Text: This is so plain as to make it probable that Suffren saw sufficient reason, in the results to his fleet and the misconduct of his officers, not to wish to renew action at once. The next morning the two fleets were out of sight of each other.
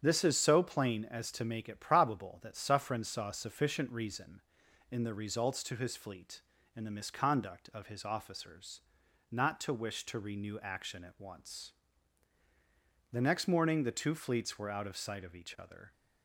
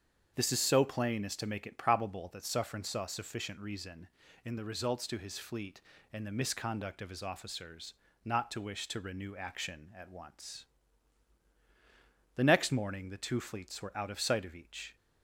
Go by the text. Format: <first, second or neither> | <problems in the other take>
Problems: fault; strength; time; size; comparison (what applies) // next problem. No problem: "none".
first | starts louder than the rest; strong; until 1.3 s; 7.5 dB; strong in the first // stops before "other"; at 14.9 s